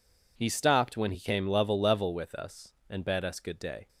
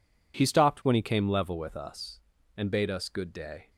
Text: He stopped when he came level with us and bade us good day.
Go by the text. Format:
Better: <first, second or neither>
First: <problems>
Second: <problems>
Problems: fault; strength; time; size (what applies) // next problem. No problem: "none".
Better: second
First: says "level" twice; at 1.7 s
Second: none